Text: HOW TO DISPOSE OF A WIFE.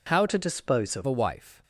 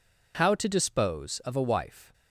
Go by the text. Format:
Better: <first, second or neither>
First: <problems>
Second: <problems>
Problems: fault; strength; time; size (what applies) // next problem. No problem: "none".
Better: second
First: changes voice from "TO" to "OF"; from 0.2 to 1.0 s; 0.8 s long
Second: none